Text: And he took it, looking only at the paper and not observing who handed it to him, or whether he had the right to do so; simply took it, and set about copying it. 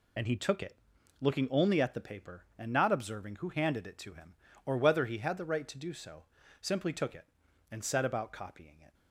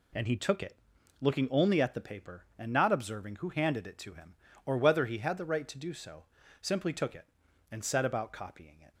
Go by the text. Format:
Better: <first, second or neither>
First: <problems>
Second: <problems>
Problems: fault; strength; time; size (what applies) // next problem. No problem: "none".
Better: second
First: loses the start of "And"; at 0.1 s; 40 ms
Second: none